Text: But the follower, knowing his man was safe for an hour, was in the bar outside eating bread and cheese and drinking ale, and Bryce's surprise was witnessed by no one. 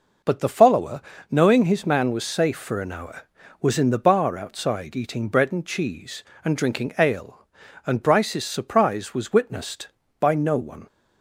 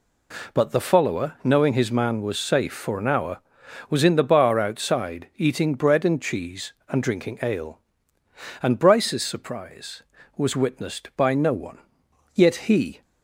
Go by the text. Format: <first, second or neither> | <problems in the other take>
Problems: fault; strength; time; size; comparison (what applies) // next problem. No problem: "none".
first | goes on to say "Yet he"; noticeable; from 12.3 s on; 0.68 s long